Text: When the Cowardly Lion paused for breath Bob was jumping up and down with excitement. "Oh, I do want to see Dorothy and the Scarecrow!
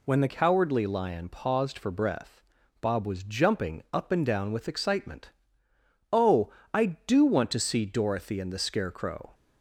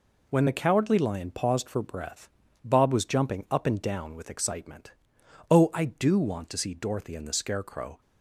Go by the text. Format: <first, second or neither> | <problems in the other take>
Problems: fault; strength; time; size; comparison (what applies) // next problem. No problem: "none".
second | changes voice at "Cowardly"; from 0.2 s on; 9.1 s long // pauses between "breath" and "Bob"; at 2.4 s; 0.38 s long; slight in the second